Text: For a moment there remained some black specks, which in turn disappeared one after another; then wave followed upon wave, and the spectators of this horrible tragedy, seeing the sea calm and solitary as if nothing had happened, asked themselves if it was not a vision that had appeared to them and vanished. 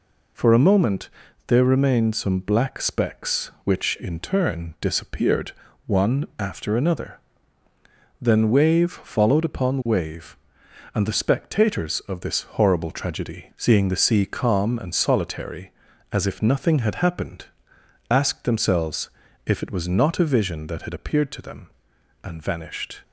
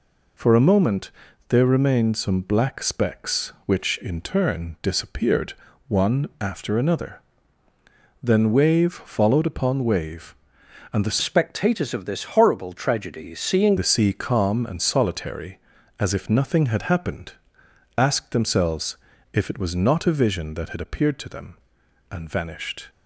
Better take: first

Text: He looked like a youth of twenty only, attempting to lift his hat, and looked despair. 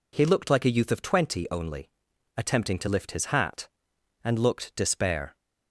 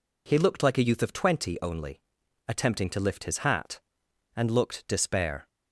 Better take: neither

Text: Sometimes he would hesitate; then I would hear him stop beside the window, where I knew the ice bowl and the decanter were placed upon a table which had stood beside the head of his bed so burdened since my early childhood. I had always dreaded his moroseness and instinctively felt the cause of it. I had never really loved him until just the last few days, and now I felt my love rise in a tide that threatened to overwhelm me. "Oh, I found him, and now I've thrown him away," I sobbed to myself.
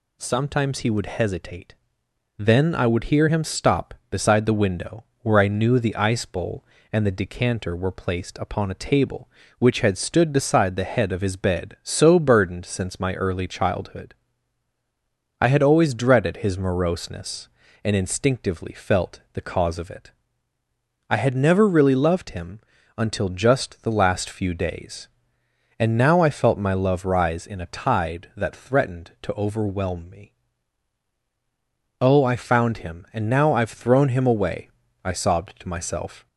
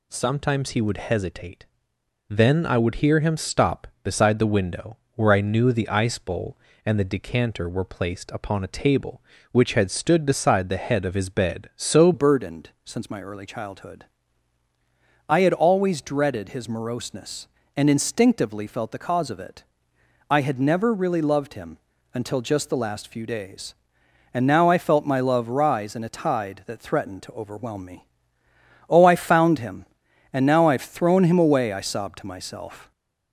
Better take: first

